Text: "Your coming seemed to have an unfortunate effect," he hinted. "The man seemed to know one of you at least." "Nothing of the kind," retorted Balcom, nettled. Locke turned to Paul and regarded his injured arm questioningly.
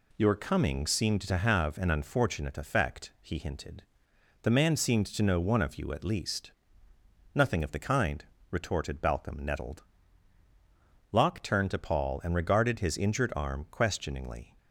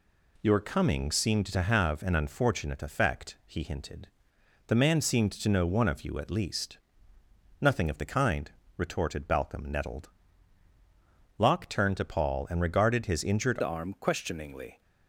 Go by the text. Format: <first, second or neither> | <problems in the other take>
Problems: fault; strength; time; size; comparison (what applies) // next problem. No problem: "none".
first | changes voice at "arm"; from 13.6 s on; 1.2 s long